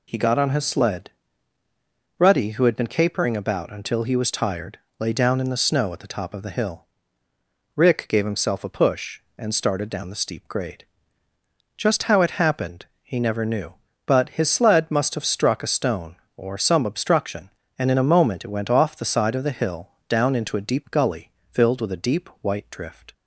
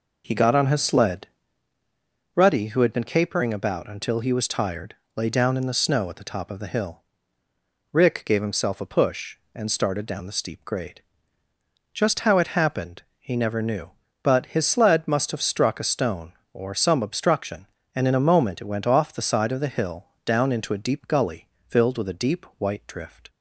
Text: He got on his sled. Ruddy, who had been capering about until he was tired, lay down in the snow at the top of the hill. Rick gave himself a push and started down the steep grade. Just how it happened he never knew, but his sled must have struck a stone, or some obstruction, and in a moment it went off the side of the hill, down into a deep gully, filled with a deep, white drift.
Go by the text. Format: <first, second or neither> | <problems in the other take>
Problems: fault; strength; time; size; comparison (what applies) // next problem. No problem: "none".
first | starts louder than the rest; noticeable; until 1.5 s; 4.5 dB // pauses between "happened" and "he"; slight; at 13.0 s; 0.16 s long; slight in the first